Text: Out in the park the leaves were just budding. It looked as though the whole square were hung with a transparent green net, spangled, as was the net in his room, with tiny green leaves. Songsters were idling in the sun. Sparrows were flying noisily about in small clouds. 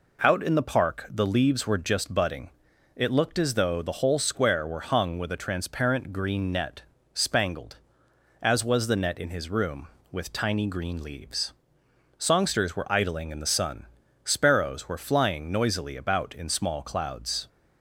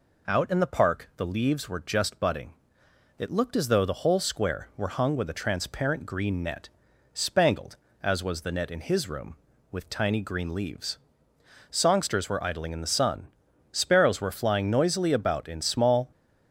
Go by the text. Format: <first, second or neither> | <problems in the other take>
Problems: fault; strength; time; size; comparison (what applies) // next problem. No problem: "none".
first | stops before "clouds"; at 16.1 s